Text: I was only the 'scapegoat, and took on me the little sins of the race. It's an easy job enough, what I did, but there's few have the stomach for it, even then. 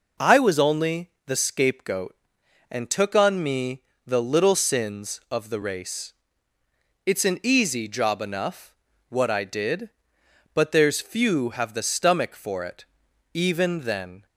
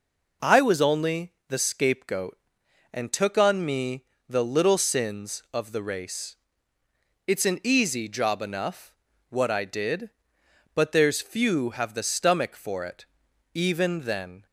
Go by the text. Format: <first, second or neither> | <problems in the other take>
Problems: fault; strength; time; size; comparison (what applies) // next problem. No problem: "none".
neither | pauses between "me" and "the"; slight; the same in both